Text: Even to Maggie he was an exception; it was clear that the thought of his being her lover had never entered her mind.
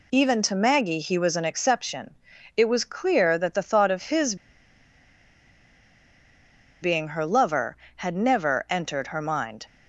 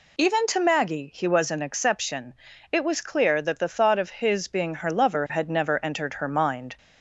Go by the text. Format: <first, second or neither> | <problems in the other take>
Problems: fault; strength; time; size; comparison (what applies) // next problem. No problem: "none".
second | pauses between "his" and "being"; strong; at 4.3 s; 2.4 s long